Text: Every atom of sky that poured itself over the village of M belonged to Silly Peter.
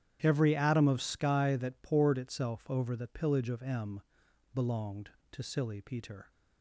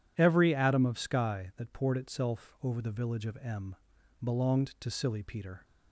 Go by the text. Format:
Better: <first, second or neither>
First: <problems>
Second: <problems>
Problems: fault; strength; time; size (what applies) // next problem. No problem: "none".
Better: second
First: starts louder than the rest; strong; until 1.2 s; 9.5 dB // says "pillage" for "village"; at 3.0 s // pauses between "M" and "belonged"; noticeable; at 4.0 s; 0.52 s long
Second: pauses between "M" and "belonged"; noticeable; at 3.7 s; 0.46 s long